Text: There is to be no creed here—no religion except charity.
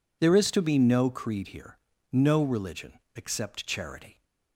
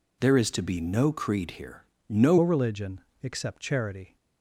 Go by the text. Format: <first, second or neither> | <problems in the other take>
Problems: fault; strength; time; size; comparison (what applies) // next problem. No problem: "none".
first | changes voice at "religion"; from 2.3 s on; 1.8 s long // pauses between "religion" and "except"; slight; at 2.9 s; 0.22 s long; slight in the first